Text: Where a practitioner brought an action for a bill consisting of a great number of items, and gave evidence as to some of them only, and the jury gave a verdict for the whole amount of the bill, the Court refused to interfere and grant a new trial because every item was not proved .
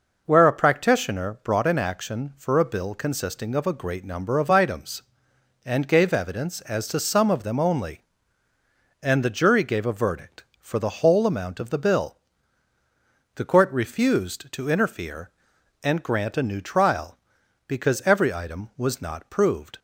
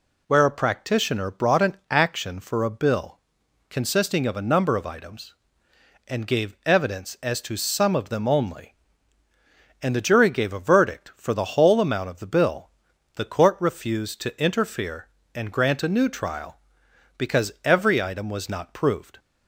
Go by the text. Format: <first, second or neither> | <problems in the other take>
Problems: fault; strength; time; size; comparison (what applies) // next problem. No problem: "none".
first | pauses between "bill" and "consisting"; noticeable; at 3.1 s; 0.50 s long // skips "great"; at 4.4 s